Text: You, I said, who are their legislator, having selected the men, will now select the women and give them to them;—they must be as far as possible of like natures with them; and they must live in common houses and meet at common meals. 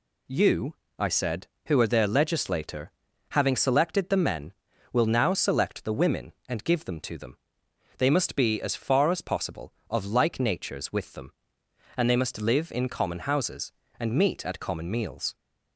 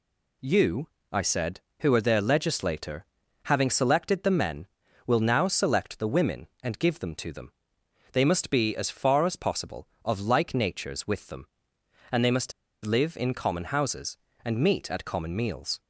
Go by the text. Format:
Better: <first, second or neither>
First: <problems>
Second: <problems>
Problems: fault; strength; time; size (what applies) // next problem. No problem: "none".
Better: first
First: none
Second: pauses between "must" and "live"; slight; at 12.5 s; 0.33 s long